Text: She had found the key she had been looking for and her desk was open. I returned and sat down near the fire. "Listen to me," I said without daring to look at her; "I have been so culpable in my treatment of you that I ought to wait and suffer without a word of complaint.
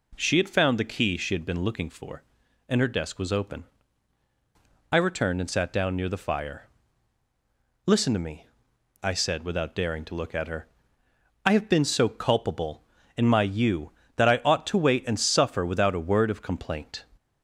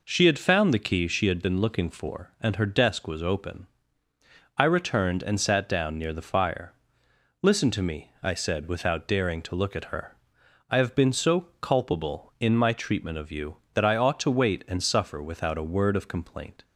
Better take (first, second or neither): second